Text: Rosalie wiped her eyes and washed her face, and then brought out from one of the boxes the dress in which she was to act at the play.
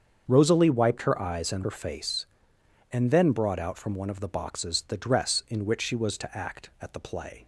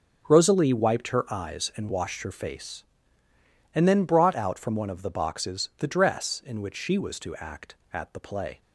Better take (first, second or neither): second